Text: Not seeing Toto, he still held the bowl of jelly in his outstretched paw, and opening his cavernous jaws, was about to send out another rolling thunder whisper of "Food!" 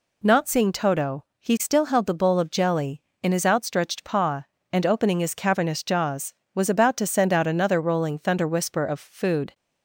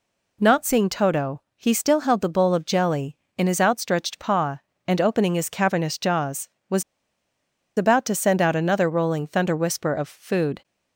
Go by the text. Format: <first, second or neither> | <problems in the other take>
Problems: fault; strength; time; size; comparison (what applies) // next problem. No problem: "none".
first | pauses between "was" and "about"; noticeable; at 6.8 s; 0.95 s long